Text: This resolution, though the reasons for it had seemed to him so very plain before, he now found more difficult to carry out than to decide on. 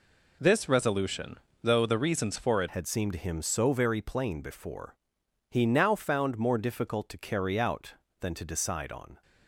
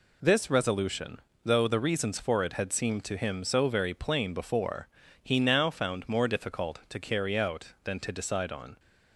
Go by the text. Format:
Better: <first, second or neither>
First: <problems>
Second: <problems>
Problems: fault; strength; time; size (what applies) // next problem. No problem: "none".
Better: second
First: changes voice at "had"; from 2.6 s on; 6.6 s long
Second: none